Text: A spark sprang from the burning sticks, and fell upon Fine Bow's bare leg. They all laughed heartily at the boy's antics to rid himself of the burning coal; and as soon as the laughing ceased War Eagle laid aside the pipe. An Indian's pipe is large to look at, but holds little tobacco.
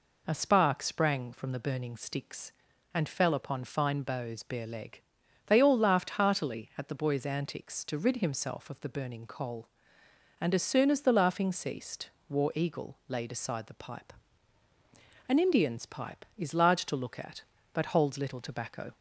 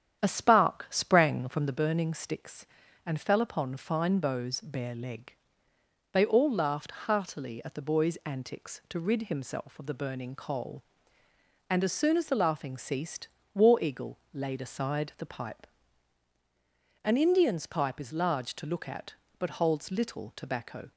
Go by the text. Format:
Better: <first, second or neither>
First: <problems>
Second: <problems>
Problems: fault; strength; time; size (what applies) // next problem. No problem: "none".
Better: first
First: pauses between "ceased" and "War"; slight; at 12.0 s; 0.18 s long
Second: starts louder than the rest; strong; until 1.8 s; 9.5 dB // pauses between "ceased" and "War"; slight; at 13.2 s; 0.26 s long